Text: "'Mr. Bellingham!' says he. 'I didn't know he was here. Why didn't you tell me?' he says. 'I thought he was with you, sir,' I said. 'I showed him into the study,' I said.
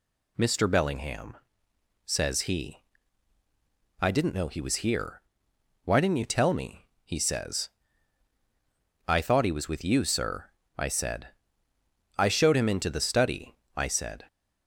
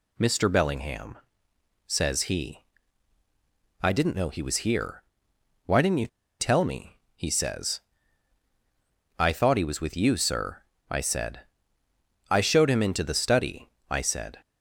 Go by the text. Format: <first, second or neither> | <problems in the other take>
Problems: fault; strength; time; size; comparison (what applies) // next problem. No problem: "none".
first | pauses between "you" and "tell"; slight; at 6.0 s; 0.33 s long